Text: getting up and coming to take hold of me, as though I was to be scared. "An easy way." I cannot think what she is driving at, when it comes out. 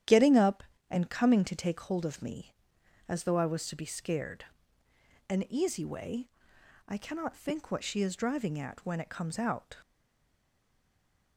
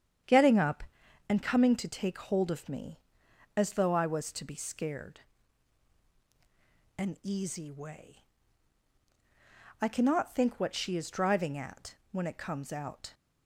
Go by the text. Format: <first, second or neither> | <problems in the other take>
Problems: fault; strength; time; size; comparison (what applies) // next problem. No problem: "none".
second | starts louder than the rest; strong; until 1.3 s; 10.5 dB; strong in the second // stays silent after the last word; noticeable; from 9.8 s on; 1.5 s long